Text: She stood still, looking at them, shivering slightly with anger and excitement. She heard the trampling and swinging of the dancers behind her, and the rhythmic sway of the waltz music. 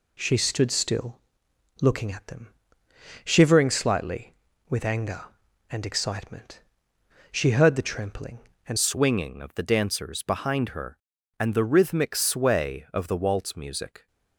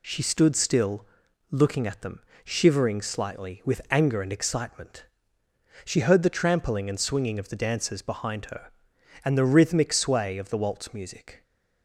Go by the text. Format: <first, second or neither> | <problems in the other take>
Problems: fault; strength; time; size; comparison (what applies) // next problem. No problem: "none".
second | changes voice at "swinging"; from 8.7 s on; 5.3 s long